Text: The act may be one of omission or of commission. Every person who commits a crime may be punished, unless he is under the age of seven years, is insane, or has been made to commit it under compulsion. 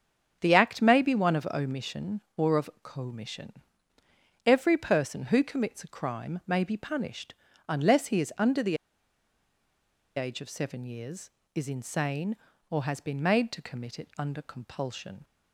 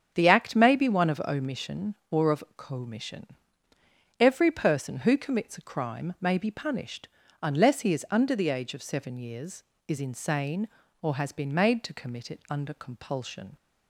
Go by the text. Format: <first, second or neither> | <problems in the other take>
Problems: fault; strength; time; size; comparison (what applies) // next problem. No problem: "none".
second | starts louder than the rest; strong; until 1.4 s; 8.5 dB; strong in the second // pauses between "the" and "age"; strong; at 8.7 s; 1.3 s long